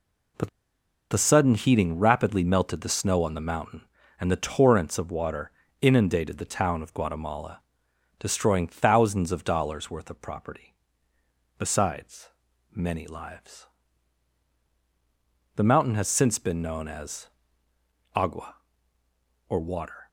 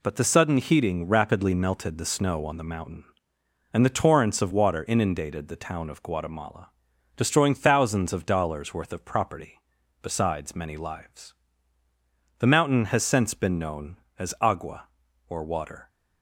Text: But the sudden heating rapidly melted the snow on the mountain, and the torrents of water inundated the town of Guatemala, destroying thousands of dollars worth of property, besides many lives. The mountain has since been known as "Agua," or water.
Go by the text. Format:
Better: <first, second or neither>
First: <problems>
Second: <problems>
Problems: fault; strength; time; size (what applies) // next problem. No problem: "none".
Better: second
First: pauses between "But" and "the"; noticeable; at 0.4 s; 0.62 s long // pauses between "water" and "inundated"; slight; at 5.5 s; 0.30 s long // pauses between "besides" and "many"; at 12.2 s; 0.44 s long // pauses between "as" and "Agua"; noticeable; at 17.2 s; 0.86 s long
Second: none